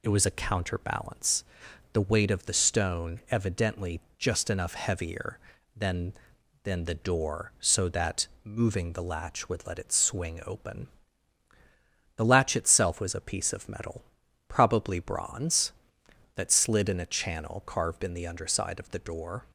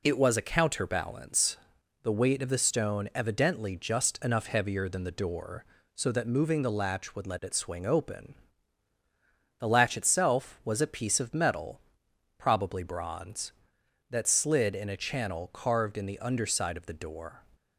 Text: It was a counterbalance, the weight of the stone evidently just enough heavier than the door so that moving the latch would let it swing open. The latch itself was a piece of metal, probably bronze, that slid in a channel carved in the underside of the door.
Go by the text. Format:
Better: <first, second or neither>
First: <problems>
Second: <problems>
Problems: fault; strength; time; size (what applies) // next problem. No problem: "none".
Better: second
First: pauses between "evidently" and "just"; slight; at 4.0 s; 0.18 s long // says "than" twice; at 6.6 s // pauses between "that" and "moving"; slight; at 8.2 s; 0.16 s long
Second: none